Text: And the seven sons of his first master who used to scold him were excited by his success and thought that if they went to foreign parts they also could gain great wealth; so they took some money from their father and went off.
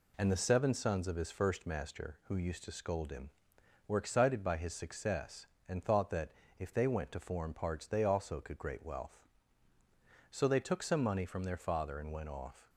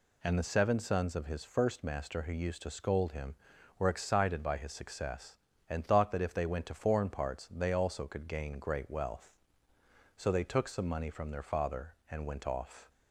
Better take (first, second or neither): second